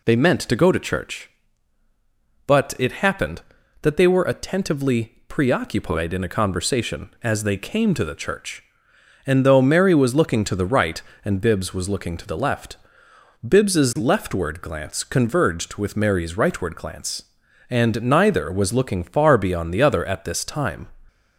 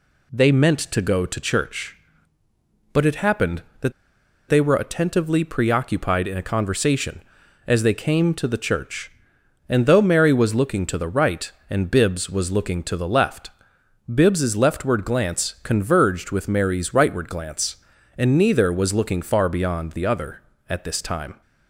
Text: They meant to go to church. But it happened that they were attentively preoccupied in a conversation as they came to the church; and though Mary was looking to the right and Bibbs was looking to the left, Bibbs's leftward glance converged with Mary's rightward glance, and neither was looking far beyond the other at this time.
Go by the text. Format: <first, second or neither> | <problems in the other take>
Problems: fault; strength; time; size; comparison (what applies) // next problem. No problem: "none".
first | pauses between "that" and "they"; noticeable; at 3.9 s; 0.56 s long